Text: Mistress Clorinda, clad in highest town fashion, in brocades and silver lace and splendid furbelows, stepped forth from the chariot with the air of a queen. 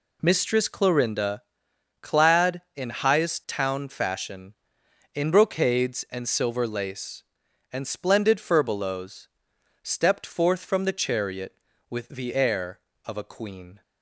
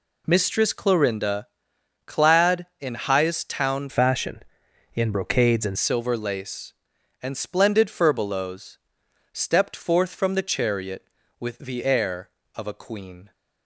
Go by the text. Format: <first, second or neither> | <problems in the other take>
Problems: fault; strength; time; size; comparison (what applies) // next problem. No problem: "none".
first | changes voice from "fashion" to "and"; from 3.8 to 5.7 s; 1.9 s long